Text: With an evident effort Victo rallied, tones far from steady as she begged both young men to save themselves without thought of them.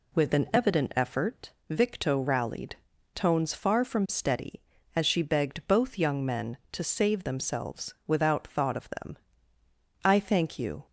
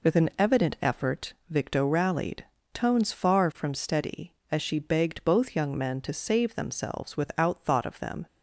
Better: second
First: pauses between "effort" and "Victo"; slight; at 1.5 s; 0.18 s long // goes on to say "I thank you"; noticeable; from 10.0 s on; 0.80 s long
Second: none

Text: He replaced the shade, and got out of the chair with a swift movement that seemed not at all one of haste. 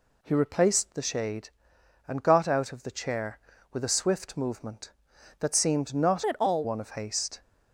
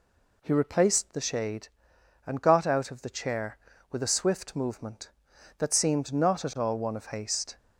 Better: second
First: changes voice from "at" to "all"; from 6.2 to 6.6 s; 0.4 s long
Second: none

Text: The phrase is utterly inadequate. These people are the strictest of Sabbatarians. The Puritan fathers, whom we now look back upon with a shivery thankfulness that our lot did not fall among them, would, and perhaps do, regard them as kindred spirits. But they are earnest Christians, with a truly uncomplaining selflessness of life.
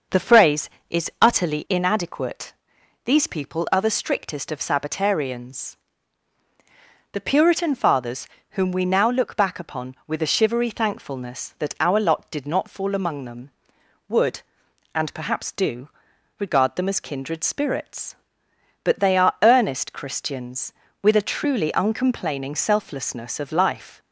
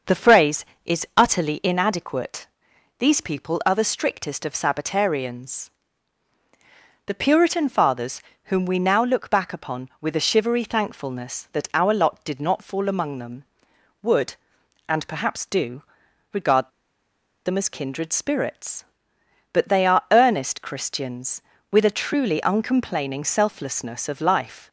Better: first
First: starts louder than the rest; noticeable; until 1.4 s; 6 dB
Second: starts louder than the rest; until 1.3 s; 6 dB // pauses between "regard" and "them"; noticeable; at 16.6 s; 0.76 s long

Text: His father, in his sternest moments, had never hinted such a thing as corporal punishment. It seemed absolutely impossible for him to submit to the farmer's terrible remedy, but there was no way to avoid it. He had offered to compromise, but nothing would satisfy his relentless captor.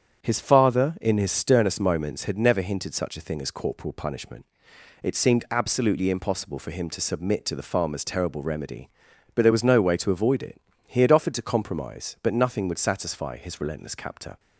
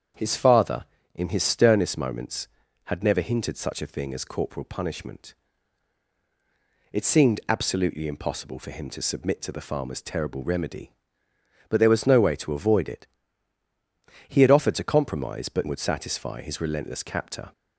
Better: first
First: starts louder than the rest; strong; until 1.2 s; 8 dB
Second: starts louder than the rest; strong; until 1.4 s; 8 dB // skips "nothing"; at 15.6 s

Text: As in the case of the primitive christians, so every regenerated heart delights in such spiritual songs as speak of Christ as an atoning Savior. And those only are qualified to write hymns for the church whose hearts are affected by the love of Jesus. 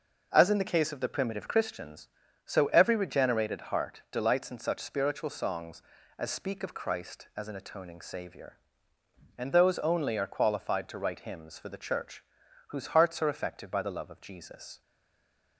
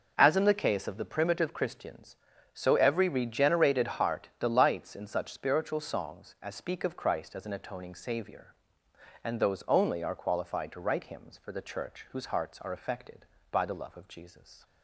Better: second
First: pauses between "church" and "whose"; noticeable; at 12.2 s; 0.46 s long // stays silent after the last word; slight; from 14.8 s on; 0.7 s long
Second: none

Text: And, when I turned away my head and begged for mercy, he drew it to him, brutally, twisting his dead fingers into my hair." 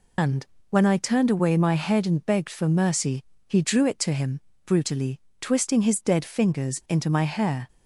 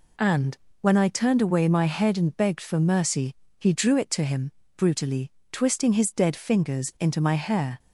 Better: second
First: loses the start of "And"; at 0.1 s; 110 ms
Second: none

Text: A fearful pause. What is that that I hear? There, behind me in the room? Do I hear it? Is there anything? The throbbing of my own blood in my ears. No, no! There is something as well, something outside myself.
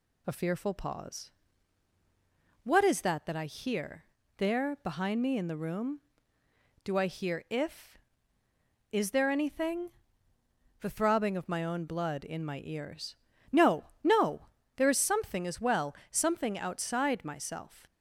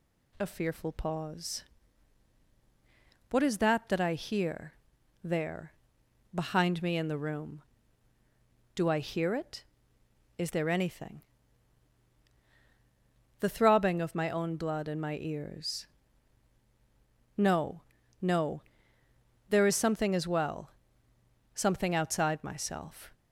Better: second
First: says "if" for "it"; at 7.4 s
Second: none

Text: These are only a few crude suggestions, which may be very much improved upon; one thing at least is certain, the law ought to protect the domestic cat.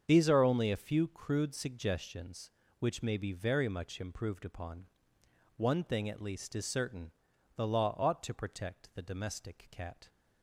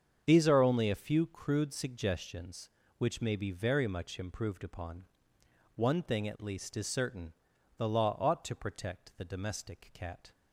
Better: neither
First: starts louder than the rest; strong; until 1.0 s; 7.5 dB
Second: starts louder than the rest; strong; until 1.2 s; 7.5 dB

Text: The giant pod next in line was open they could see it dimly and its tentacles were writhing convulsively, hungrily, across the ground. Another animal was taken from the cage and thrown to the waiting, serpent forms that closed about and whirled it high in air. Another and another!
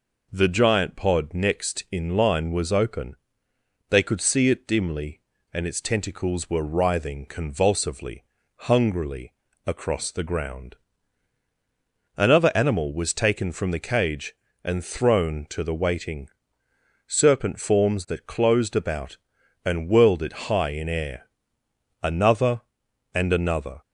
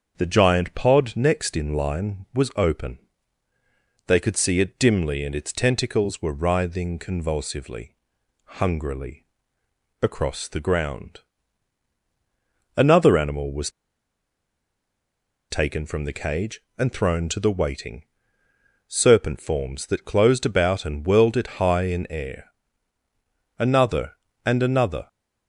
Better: first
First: pauses between "open" and "they"; noticeable; at 3.1 s; 0.74 s long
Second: starts louder than the rest; until 1.2 s; 7 dB // pauses between "open" and "they"; at 2.9 s; 1.0 s long // pauses between "was" and "taken"; strong; at 13.7 s; 1.7 s long

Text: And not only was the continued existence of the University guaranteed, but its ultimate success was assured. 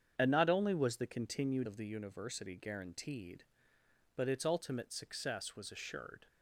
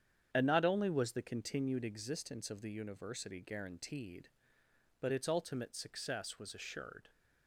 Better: second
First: starts louder than the rest; strong; until 1.1 s; 8 dB // skips "existence"; at 1.6 s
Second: starts louder than the rest; strong; until 1.3 s; 8.5 dB

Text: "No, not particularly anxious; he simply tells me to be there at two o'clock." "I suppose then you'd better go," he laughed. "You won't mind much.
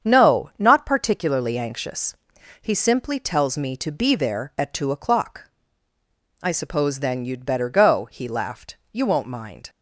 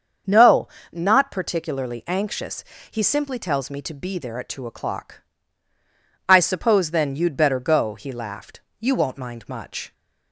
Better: second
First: starts louder than the rest; strong; until 1.1 s; 8 dB // stops before "much"; at 9.6 s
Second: starts louder than the rest; until 1.5 s; 7 dB

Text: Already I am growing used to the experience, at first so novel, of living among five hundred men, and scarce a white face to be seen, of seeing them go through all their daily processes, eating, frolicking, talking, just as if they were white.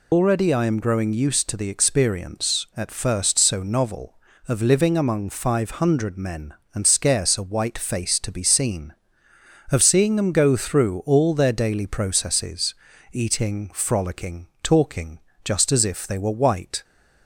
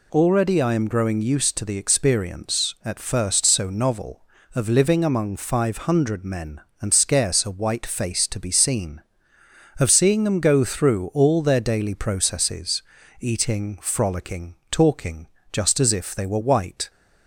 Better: second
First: loses the start of "Already"; at 0.1 s; 85 ms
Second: none

